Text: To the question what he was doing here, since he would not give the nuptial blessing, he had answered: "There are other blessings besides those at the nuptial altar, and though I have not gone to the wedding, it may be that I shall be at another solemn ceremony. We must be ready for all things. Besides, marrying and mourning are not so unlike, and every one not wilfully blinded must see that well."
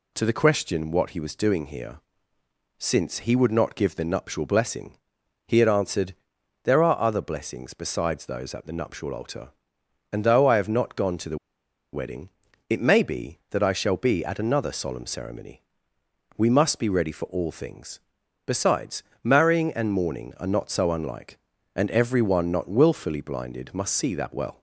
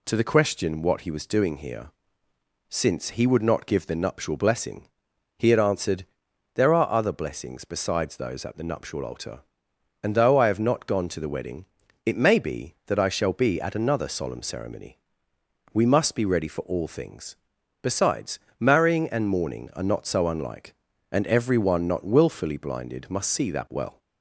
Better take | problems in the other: second | pauses between "the" and "wedding"; noticeable; at 11.3 s; 0.55 s long

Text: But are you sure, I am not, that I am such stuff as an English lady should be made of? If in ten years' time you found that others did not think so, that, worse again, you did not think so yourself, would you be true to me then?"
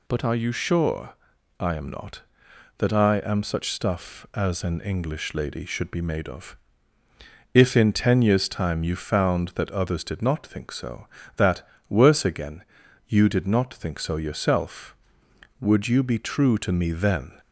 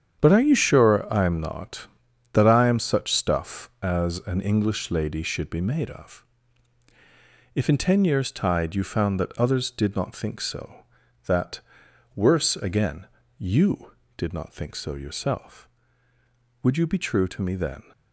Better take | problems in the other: first | starts louder than the rest; strong; until 1.2 s; 8.5 dB // says "tide" for "time"; at 8.3 s

